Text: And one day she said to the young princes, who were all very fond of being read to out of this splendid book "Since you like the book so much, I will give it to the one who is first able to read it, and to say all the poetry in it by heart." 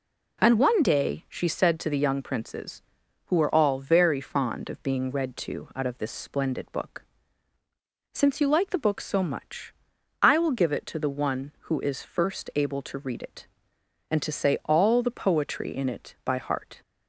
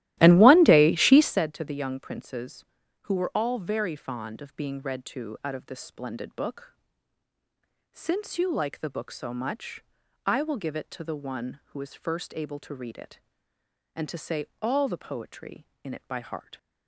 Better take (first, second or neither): first